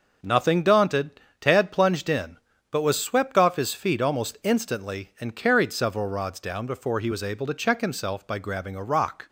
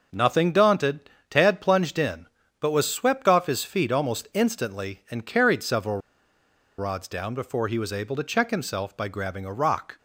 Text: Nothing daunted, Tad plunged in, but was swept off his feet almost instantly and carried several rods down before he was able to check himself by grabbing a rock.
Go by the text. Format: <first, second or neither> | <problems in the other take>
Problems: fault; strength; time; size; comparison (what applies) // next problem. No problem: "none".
first | starts louder than the rest; noticeable; until 1.3 s; 6 dB // pauses between "several" and "rods"; noticeable; at 5.9 s; 0.80 s long